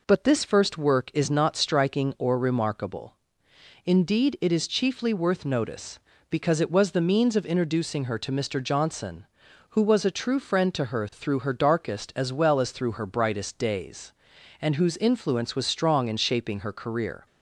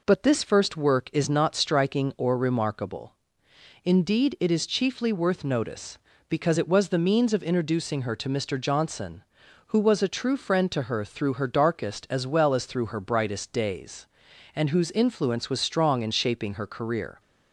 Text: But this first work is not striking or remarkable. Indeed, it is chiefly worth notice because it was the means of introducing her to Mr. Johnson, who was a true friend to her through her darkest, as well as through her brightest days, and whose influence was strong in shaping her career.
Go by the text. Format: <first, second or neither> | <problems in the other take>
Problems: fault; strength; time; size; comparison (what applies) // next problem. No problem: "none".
neither | none